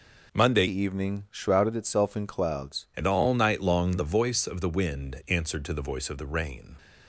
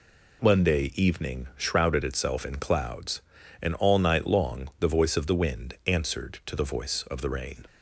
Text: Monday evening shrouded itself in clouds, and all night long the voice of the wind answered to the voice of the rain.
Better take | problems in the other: second | changes voice from "evening" to "clouds"; from 0.6 to 2.8 s; 2.2 s long

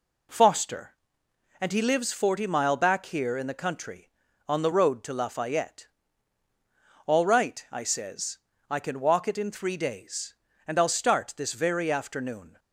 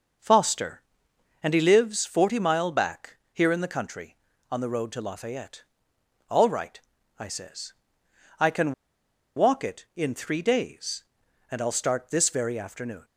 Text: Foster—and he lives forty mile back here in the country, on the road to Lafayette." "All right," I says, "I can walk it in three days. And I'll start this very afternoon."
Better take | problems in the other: first | starts louder than the rest; noticeable; until 1.8 s; 6 dB // pauses between "back" and "here"; slight; at 3.1 s; 0.16 s long // pauses between "can" and "walk"; noticeable; at 8.7 s; 0.62 s long

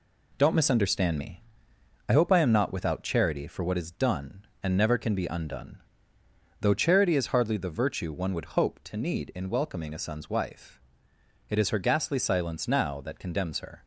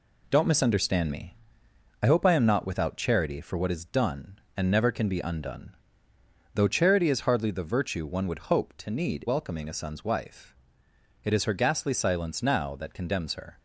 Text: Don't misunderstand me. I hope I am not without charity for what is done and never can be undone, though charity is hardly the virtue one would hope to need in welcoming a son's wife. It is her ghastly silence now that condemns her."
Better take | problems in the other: first | skips "in"; at 9.2 s

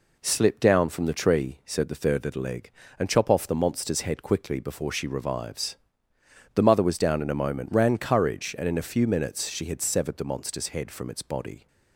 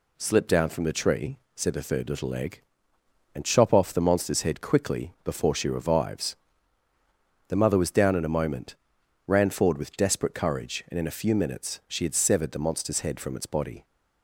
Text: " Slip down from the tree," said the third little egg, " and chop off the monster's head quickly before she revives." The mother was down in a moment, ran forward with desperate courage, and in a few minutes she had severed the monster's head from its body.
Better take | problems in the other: second | skips "forward with desperate"; at 7.9 s

